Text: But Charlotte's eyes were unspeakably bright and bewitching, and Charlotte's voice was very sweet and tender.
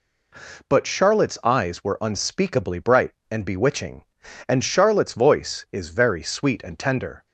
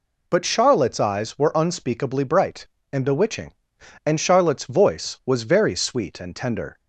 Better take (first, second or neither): second